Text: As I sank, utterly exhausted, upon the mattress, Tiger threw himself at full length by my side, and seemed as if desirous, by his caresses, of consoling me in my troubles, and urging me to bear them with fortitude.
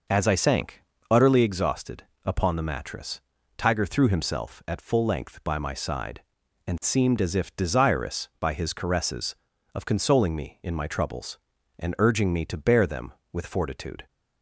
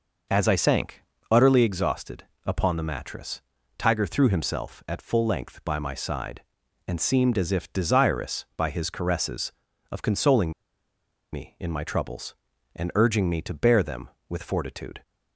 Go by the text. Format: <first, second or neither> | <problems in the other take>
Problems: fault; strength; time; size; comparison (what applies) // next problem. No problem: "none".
first | pauses between "consoling" and "me"; noticeable; at 10.5 s; 0.82 s long